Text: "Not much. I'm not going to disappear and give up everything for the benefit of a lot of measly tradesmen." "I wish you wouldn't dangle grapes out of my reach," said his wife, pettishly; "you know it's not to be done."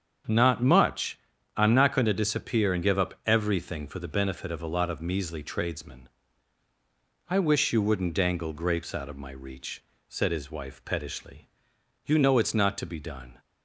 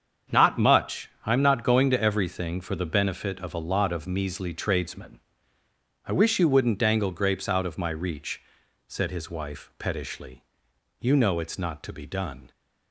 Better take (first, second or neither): first